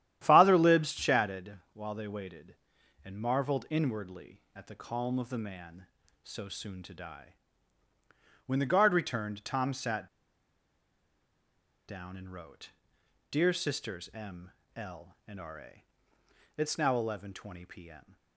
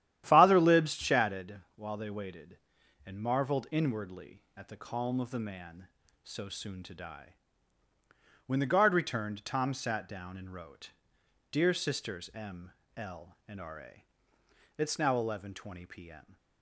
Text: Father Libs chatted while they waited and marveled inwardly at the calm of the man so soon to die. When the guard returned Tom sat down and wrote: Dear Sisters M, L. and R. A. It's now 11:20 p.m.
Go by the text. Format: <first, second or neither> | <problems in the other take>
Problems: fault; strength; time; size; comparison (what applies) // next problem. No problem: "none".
second | starts louder than the rest; strong; until 1.2 s; 11.5 dB; strong in the second // pauses between "chatted" and "while"; slight; at 1.5 s; 0.20 s long; slight in the second // pauses between "sat" and "down"; strong; at 10.0 s; 1.8 s long // pauses between "A" and "It's"; noticeable; at 15.8 s; 0.74 s long; noticeable in the second